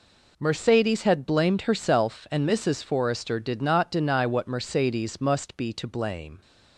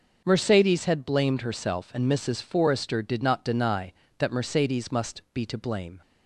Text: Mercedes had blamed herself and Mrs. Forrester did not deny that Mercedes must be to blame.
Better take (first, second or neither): second